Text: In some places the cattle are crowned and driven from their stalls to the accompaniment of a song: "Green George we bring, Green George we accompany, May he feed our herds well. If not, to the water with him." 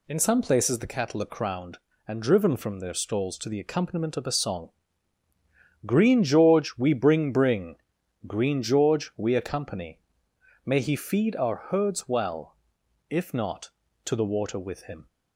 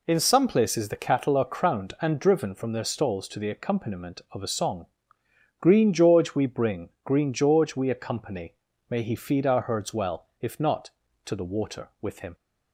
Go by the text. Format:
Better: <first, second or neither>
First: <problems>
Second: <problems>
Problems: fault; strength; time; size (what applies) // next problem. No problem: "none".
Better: second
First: says "bring" twice; at 7.3 s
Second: none